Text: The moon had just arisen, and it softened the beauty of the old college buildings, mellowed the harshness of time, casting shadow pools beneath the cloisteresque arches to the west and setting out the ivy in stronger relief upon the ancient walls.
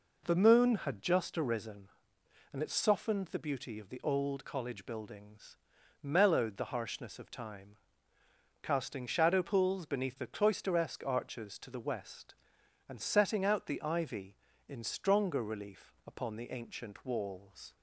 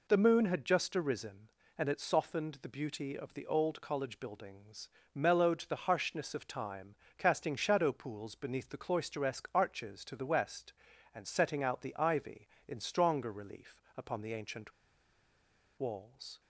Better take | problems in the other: first | pauses between "ancient" and "walls"; at 14.7 s; 1.0 s long

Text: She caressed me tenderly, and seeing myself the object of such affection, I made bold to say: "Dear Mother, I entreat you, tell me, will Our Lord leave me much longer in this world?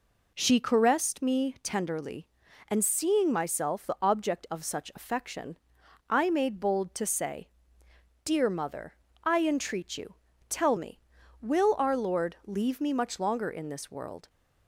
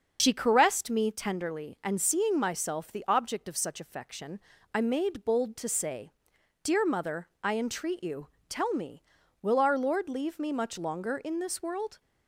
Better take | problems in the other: first | loses the start of "She"; at 0.1 s; 60 ms // starts louder than the rest; until 1.2 s; 6.5 dB

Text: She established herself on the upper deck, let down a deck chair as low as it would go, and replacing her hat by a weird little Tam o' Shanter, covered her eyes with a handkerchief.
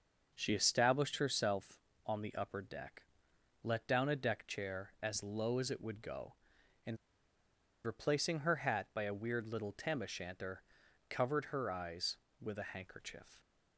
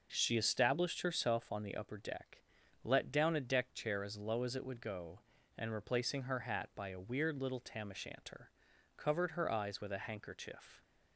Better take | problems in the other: second | pauses between "and" and "replacing"; noticeable; at 6.9 s; 0.89 s long

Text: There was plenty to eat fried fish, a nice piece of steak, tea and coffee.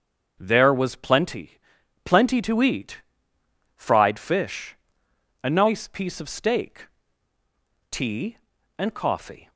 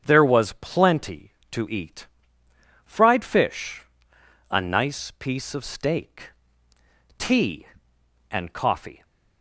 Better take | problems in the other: second | starts louder than the rest; until 1.3 s; 7 dB; strong in the second // says "plenty" twice; at 2.0 s // pauses between "eat" and "fried"; noticeable; at 3.0 s; 0.74 s long; noticeable in the second

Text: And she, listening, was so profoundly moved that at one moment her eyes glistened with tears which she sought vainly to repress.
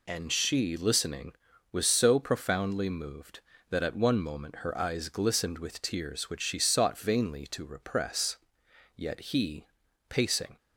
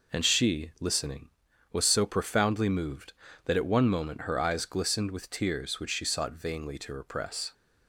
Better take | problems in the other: second | goes on to say "Yet he pacing"; from 8.9 s on; 1.6 s long

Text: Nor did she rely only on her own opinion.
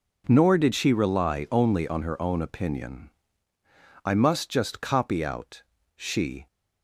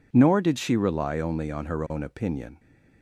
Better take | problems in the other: second | goes on to say "I must just copy out she"; strong; from 4.0 s on; 2.4 s long

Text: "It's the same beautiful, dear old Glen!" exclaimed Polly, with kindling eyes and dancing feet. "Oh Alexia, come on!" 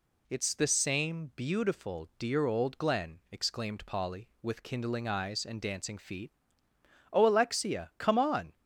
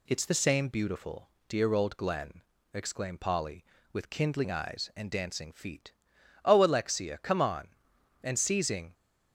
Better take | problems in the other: first | goes on to say "and seizing"; noticeable; from 8.2 s on; 0.72 s long

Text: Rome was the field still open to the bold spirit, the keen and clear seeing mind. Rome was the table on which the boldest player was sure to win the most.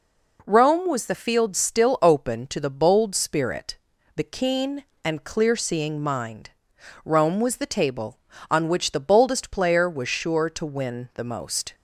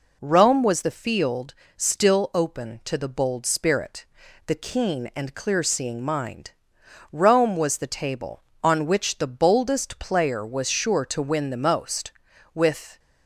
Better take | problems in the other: first | pauses between "field" and "still"; slight; at 1.5 s; 0.24 s long // goes on to say "With"; slight; from 12.5 s on; 0.46 s long

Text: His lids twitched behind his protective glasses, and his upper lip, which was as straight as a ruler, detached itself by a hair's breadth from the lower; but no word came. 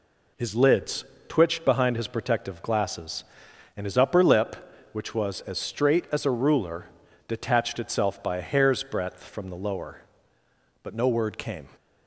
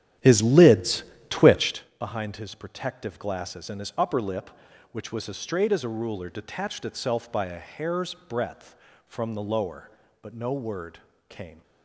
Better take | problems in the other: first | starts louder than the rest; strong; until 1.8 s; 11.5 dB // pauses between "lids" and "twitched"; slight; at 1.0 s; 0.28 s long; slight in the first // pauses between "word" and "came"; slight; at 10.9 s; 0.30 s long

